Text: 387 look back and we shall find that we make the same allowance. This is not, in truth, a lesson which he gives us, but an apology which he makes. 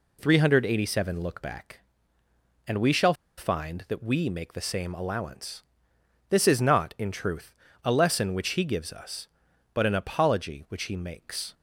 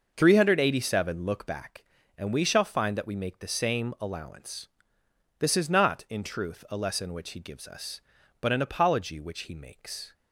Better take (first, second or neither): second